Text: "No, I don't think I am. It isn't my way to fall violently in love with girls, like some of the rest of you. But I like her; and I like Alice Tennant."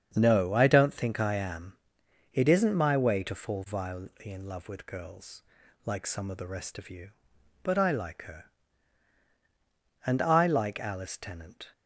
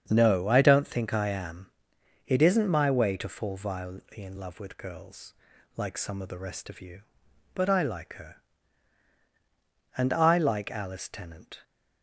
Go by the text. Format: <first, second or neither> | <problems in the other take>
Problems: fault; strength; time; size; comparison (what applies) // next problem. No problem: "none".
neither | starts louder than the rest; strong; the same in both